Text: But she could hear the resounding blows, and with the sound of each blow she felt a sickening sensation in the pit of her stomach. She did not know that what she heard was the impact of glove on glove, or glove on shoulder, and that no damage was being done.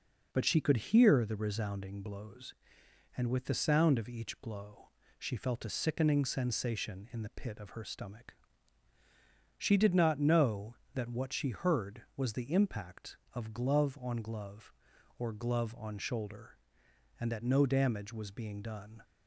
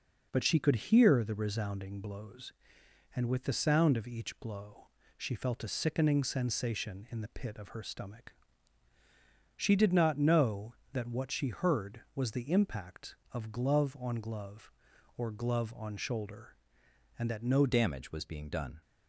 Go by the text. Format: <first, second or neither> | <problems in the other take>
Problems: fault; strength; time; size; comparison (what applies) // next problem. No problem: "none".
first | pauses between "blow" and "she"; slight; at 4.8 s; 0.28 s long; slight in the first // changes voice at "damage"; from 17.6 s on; 1.2 s long